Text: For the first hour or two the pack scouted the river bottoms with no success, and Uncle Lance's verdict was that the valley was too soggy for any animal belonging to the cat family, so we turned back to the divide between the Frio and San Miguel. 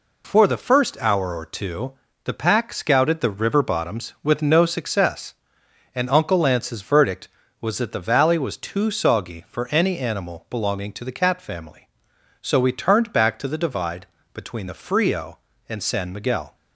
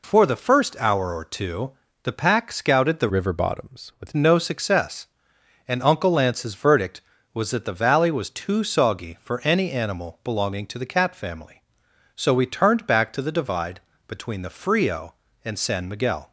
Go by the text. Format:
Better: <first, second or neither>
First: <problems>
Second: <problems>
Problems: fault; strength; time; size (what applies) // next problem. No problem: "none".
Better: first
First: pauses between "two" and "the"; slight; at 1.9 s; 0.32 s long // pauses between "divide" and "between"; slight; at 14.0 s; 0.26 s long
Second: pauses between "two" and "the"; slight; at 1.7 s; 0.32 s long // changes voice from "river" to "with"; from 3.0 to 4.1 s; 1.1 s long // pauses between "divide" and "between"; slight; at 13.8 s; 0.26 s long